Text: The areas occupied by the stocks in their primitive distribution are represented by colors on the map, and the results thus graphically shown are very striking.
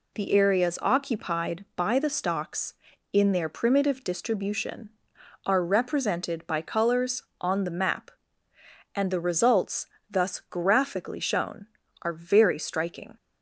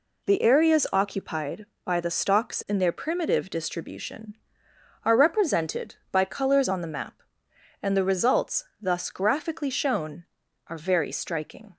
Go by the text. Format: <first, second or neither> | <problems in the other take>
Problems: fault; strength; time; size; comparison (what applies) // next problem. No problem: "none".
neither | pauses between "results" and "thus"; slight; the same in both